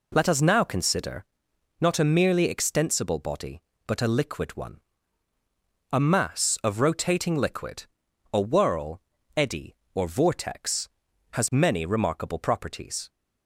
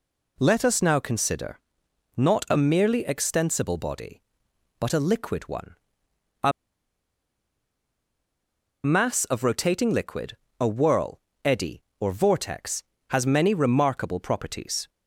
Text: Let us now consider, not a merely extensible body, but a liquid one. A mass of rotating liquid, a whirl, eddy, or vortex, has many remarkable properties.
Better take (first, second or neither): first